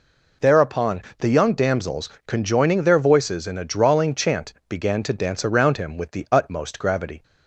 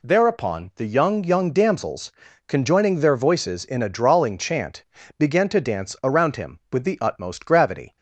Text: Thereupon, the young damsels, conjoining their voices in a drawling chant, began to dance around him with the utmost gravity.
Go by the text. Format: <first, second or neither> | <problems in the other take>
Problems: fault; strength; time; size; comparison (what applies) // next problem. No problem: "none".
first | says "young" twice; at 1.2 s